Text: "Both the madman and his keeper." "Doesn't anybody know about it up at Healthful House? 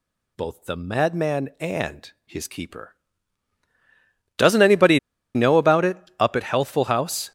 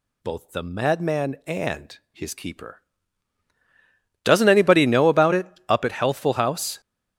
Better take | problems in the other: second | pauses between "anybody" and "know"; at 4.9 s; 0.36 s long // pauses between "it" and "up"; slight; at 5.9 s; 0.20 s long; slight in the second

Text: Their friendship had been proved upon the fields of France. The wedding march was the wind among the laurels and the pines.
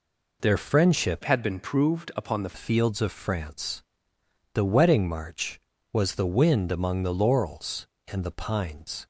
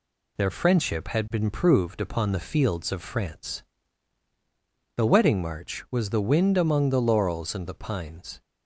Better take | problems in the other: second | changes voice from "had" to "the"; from 1.2 to 2.5 s; 1.3 s long

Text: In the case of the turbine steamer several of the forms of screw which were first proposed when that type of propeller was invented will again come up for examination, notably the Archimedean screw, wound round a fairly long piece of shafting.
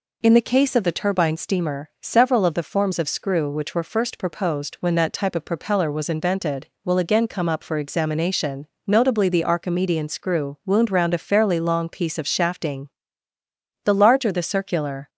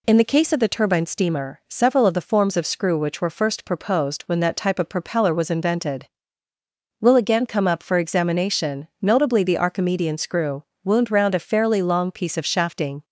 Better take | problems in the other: second | goes on to say "The larger the circular"; noticeable; from 13.8 s on; 1.2 s long

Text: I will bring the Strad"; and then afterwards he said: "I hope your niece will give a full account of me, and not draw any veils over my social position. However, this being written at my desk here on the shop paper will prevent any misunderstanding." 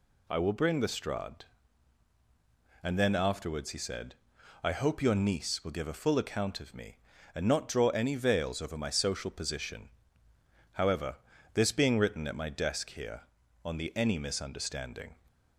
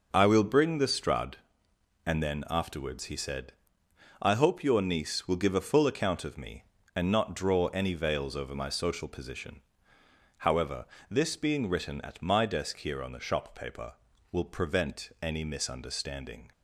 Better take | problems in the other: second | skips "shop paper will prevent"; at 13.9 s

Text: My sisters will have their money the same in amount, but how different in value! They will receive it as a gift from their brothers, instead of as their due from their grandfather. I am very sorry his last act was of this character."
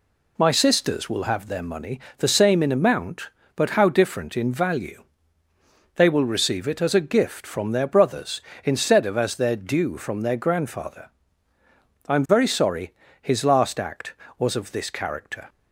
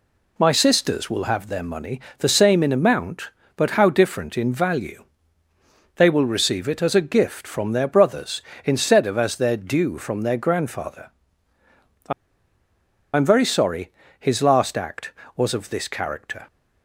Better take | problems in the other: first | pauses between "money" and "the"; slight; at 1.9 s; 0.18 s long; slight in the first // pauses between "I" and "am"; at 12.1 s; 1.0 s long // pauses between "sorry" and "his"; slight; at 13.9 s; 0.26 s long; slight in the first

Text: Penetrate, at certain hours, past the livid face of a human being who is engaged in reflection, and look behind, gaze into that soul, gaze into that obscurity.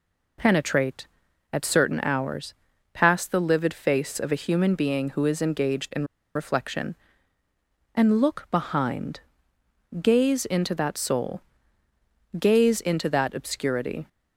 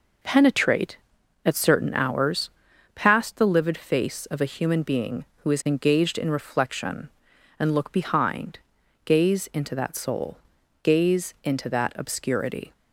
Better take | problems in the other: second | pauses between "in" and "reflection"; slight; at 6.0 s; 0.30 s long

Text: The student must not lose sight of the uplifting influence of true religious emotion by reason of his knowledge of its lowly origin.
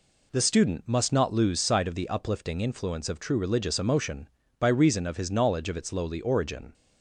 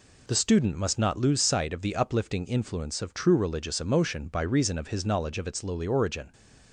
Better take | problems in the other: neither | none

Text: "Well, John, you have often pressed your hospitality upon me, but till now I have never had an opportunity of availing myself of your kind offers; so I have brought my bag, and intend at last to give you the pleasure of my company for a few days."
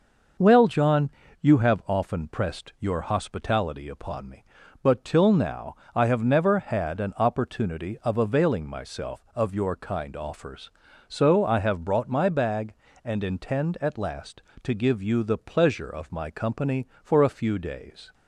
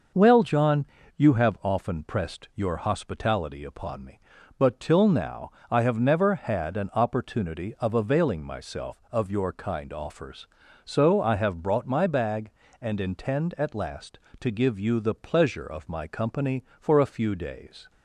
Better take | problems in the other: neither | pauses between "now" and "I"; slight; the same in both

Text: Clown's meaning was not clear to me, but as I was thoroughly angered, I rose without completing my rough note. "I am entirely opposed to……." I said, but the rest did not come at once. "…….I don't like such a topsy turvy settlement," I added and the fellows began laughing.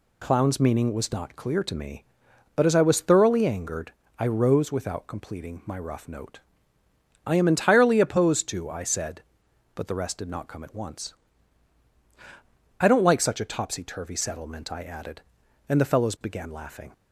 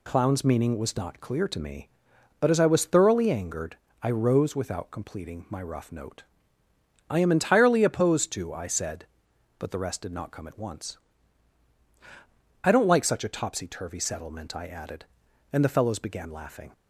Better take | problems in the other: neither | none

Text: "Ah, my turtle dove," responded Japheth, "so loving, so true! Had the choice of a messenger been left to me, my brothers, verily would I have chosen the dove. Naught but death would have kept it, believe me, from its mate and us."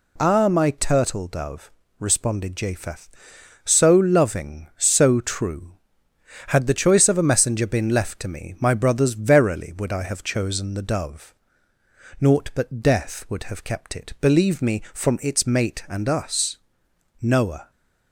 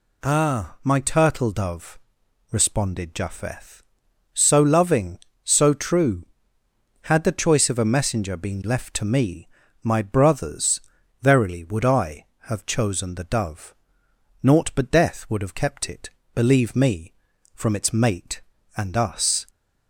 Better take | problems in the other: second | goes on to say "Noah"; from 17.2 s on; 0.50 s long

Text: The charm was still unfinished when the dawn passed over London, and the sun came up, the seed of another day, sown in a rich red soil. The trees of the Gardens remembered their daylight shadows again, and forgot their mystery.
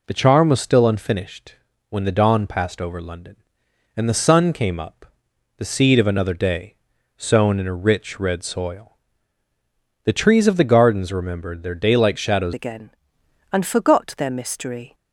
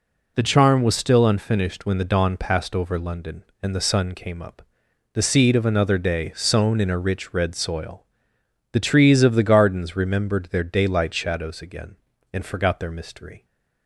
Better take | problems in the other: second | pauses between "unfinished" and "when"; slight; at 1.5 s; 0.34 s long // changes voice at "again"; from 12.5 s on; 2.4 s long

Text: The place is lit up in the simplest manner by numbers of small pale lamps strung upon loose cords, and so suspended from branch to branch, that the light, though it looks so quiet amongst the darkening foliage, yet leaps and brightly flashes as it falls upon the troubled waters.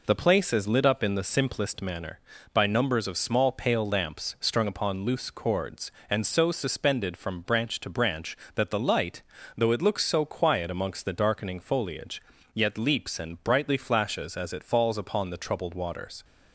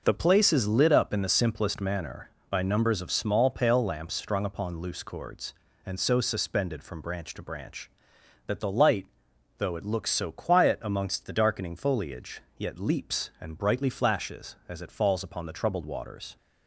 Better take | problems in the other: first | changes voice at "place"; from 0.1 s on; 16.2 s long

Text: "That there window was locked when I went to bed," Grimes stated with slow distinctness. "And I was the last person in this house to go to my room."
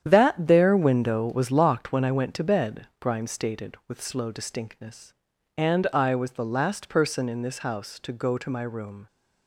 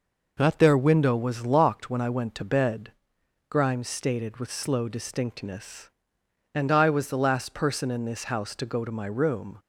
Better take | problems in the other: second | gets quieter; strong; throughout; 9.5 dB

